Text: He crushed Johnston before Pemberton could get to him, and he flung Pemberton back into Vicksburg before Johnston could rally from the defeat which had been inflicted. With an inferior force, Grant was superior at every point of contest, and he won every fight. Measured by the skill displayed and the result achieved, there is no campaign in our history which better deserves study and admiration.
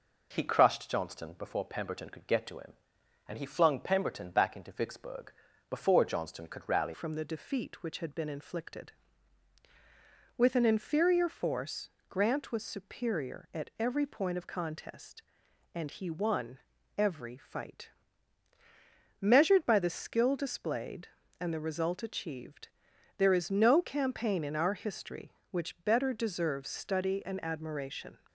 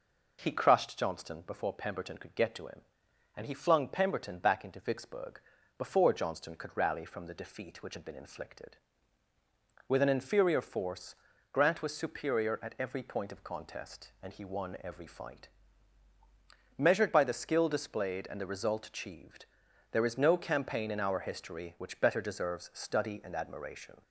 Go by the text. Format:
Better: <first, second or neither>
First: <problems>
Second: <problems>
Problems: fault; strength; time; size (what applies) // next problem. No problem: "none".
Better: second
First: pauses between "Vicksburg" and "before"; at 5.3 s; 0.38 s long // changes voice at "from"; from 6.9 s on; 21.2 s long // pauses between "won" and "every"; at 16.5 s; 0.40 s long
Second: pauses between "Vicksburg" and "before"; at 5.3 s; 0.38 s long